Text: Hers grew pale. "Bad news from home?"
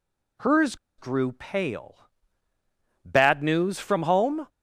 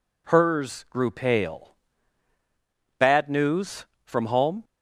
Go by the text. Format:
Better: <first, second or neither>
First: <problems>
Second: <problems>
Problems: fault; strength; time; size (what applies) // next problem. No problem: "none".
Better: second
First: pauses between "Hers" and "grew"; slight; at 0.7 s; 0.22 s long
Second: none